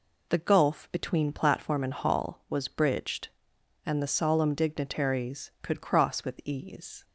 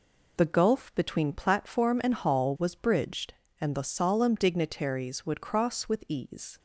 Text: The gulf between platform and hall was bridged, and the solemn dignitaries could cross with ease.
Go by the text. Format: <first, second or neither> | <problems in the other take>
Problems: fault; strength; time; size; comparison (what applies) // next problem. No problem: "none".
first | says "would" for "could"; at 5.2 s